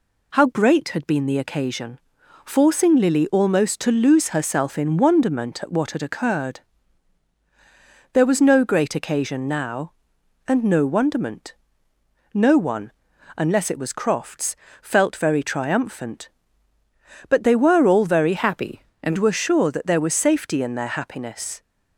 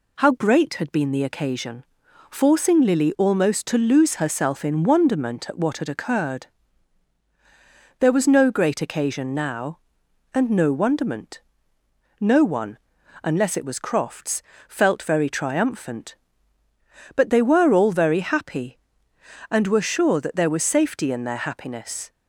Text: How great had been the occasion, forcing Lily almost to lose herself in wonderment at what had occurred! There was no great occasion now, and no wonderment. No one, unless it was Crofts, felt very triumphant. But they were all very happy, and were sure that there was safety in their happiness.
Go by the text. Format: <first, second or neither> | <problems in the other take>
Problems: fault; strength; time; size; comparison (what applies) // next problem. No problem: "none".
second | changes voice from "happy" to "and"; from 18.3 to 19.1 s; 0.8 s long